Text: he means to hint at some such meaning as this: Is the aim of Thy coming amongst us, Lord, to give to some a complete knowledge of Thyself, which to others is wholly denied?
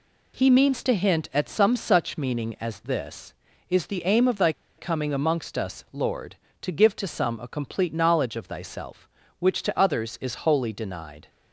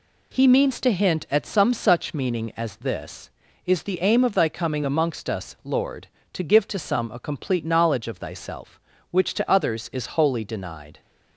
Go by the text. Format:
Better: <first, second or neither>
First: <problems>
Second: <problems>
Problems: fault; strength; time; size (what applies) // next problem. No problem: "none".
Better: second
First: pauses between "Thy" and "coming"; slight; at 4.5 s; 0.27 s long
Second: none